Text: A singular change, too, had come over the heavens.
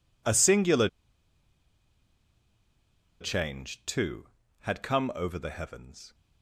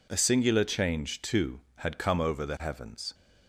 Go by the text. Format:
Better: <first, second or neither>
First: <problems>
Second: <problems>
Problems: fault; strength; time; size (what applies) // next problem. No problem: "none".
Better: second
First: pauses between "singular" and "change"; strong; at 0.8 s; 2.3 s long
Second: none